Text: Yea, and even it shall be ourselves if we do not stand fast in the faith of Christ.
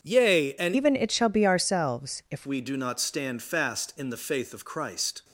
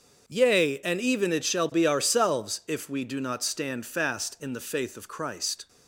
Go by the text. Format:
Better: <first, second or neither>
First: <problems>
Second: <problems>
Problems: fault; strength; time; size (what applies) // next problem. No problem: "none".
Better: second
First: starts louder than the rest; until 1.0 s; 7 dB // changes voice from "even" to "if"; from 0.7 to 2.4 s; 1.7 s long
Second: starts louder than the rest; until 1.2 s; 6.5 dB